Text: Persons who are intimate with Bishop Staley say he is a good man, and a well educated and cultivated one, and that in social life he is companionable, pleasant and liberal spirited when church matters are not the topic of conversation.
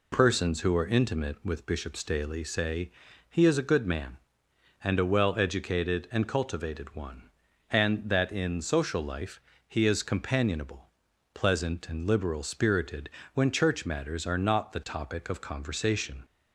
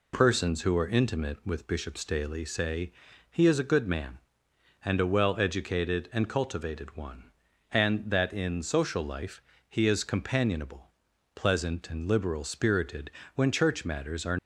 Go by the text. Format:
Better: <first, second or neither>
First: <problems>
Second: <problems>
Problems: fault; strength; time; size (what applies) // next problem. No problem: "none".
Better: first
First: pauses between "say" and "he"; at 2.9 s; 0.40 s long // pauses between "life" and "he"; slight; at 9.3 s; 0.28 s long // pauses between "spirited" and "when"; slight; at 13.0 s; 0.24 s long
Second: pauses between "say" and "he"; at 2.9 s; 0.40 s long // pauses between "life" and "he"; slight; at 9.4 s; 0.28 s long // pauses between "spirited" and "when"; slight; at 13.1 s; 0.24 s long // stops before "not the topic of conversation"; at 14.3 s